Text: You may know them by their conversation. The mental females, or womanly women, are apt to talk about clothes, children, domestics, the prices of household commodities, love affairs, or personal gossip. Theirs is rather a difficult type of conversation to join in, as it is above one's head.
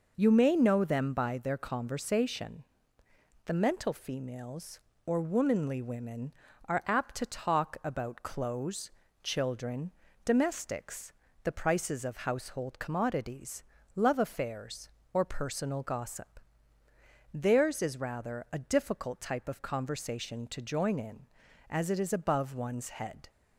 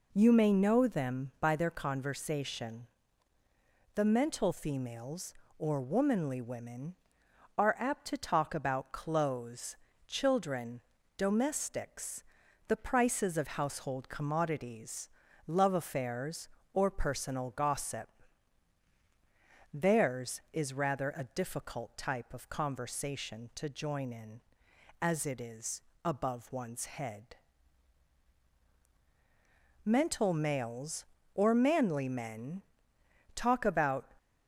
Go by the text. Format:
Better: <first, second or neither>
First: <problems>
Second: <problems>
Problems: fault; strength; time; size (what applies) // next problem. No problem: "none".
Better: first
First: none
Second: pauses between "is" and "above"; slight; at 25.8 s; 0.22 s long // goes on to say "Mental males or manly men talk about"; strong; from 29.8 s on; 4.2 s long